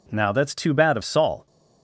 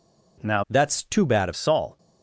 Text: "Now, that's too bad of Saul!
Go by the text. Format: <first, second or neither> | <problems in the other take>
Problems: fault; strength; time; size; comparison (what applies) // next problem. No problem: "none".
first | changes voice from "that's" to "of"; from 0.6 to 1.5 s; 0.9 s long